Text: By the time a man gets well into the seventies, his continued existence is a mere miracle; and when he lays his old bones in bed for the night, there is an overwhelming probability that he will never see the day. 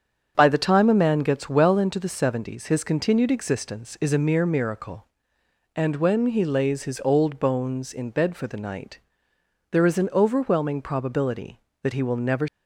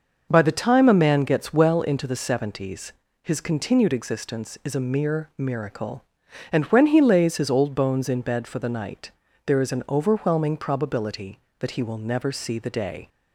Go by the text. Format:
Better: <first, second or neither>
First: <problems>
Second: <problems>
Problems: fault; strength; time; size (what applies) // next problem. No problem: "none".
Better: second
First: starts louder than the rest; strong; until 1.3 s; 7.5 dB // stops before "see the day"; at 12.4 s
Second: none